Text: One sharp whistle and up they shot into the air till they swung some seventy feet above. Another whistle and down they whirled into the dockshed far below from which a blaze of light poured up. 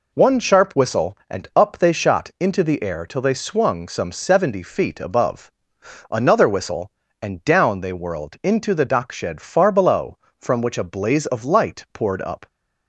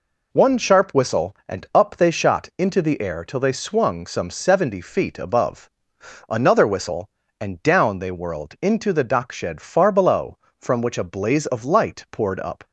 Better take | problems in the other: neither | none

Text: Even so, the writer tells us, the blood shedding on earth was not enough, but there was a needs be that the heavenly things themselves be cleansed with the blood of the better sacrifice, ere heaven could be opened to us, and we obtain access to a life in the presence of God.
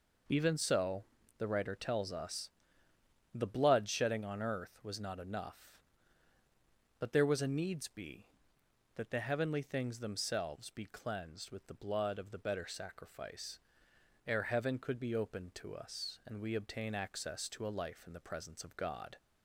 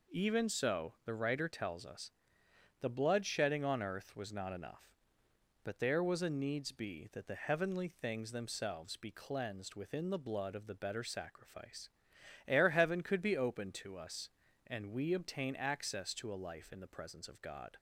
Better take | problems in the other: first | says "within" for "with"; at 9.7 s

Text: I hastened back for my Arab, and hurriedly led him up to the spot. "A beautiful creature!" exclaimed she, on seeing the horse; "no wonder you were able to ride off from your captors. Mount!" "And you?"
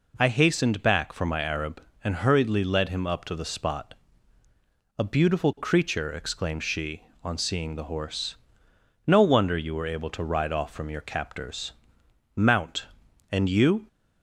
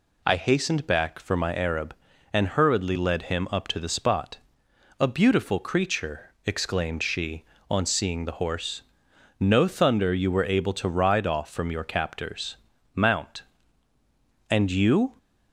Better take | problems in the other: first | says "thunder" for "wonder"; at 9.6 s

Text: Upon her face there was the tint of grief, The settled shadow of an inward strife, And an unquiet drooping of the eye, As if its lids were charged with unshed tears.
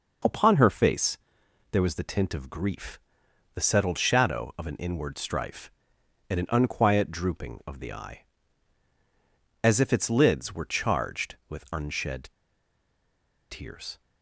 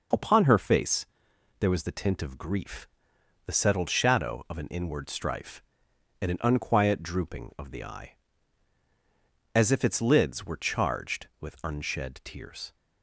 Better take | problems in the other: second | pauses between "face" and "there"; noticeable; at 1.1 s; 0.54 s long; noticeable in the second // pauses between "unshed" and "tears"; at 12.2 s; 1.2 s long

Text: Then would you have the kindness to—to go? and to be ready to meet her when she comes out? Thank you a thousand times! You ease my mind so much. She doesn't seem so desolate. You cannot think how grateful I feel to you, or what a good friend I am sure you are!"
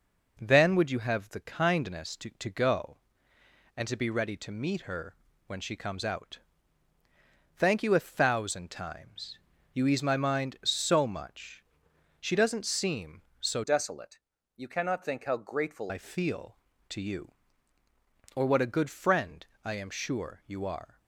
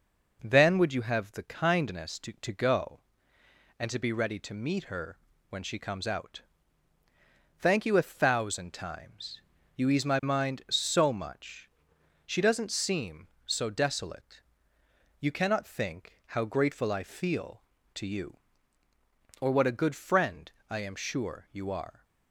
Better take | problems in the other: second | pauses between "her" and "when"; slight; at 5.1 s; 0.32 s long; slight in the second // changes voice from "desolate" to "grateful"; from 13.6 to 15.9 s; 2.3 s long // pauses between "friend" and "I"; slight; at 19.4 s; 0.20 s long; slight in the second

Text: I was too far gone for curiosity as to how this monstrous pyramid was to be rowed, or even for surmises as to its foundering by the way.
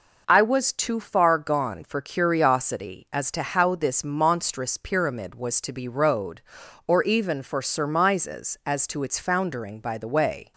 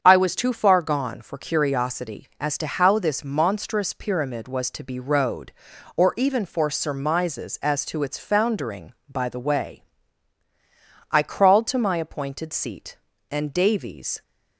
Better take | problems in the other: first | starts louder than the rest; strong; until 1.0 s; 7.5 dB // goes on to say "I crawled to my appointed seat and Davies"; strong; from 11.1 s on; 3.1 s long

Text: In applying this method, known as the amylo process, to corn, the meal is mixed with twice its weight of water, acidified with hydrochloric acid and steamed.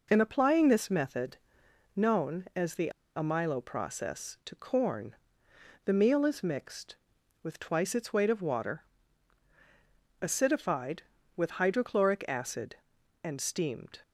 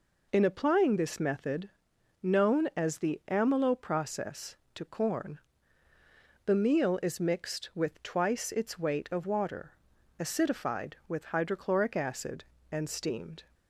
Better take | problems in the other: second | pauses between "the" and "amylo"; slight; at 2.8 s; 0.26 s long

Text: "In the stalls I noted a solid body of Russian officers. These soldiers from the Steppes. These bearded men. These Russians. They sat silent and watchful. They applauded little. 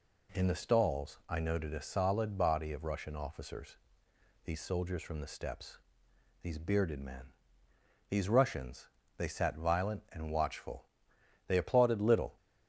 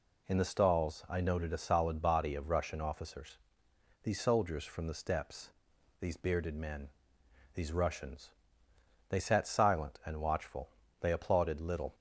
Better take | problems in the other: second | says "violent" for "silent"; at 9.5 s

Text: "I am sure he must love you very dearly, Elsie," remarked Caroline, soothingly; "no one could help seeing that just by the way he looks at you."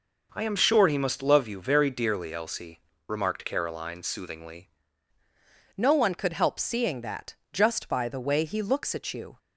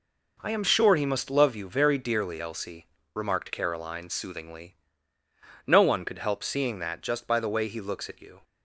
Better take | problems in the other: second | changes voice at "no"; from 5.7 s on; 3.6 s long // pauses between "that" and "just"; slight; at 7.3 s; 0.18 s long

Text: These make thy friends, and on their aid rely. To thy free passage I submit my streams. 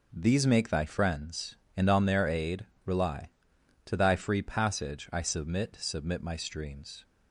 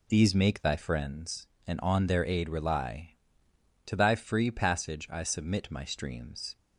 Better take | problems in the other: second | pauses between "aid" and "rely"; slight; at 2.6 s; 0.20 s long // says "submit" twice; at 5.7 s

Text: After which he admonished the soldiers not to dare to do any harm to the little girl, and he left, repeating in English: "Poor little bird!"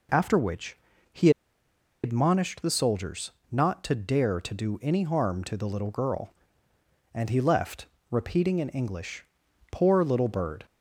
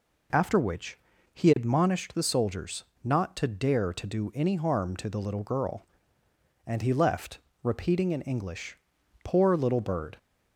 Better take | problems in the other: second | pauses between "which" and "he"; slight; at 0.7 s; 0.36 s long; slight in the second // pauses between "he" and "admonished"; noticeable; at 1.2 s; 0.73 s long // pauses between "soldiers" and "not"; slight; at 3.3 s; 0.20 s long; slight in the second

